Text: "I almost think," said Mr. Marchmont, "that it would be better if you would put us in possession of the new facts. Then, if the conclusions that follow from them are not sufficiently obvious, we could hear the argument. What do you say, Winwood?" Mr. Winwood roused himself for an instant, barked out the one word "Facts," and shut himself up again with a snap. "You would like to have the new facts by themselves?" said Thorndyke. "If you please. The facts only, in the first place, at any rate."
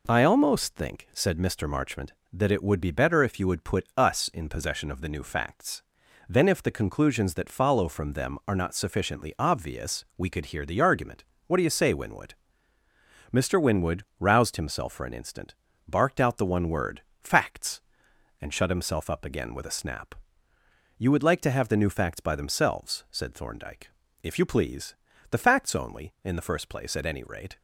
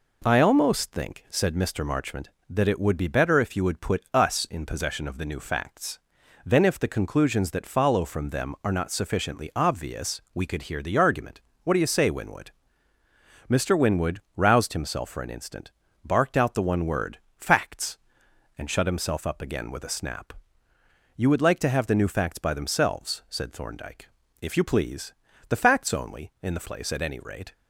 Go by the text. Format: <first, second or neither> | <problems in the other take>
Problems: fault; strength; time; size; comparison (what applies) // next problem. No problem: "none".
first | pauses between "Winwood" and "roused"; slight; at 14.2 s; 0.16 s long; slight in the first // pauses between "word" and "Facts"; slight; at 17.1 s; 0.22 s long; slight in the first // skips "first"; at 26.6 s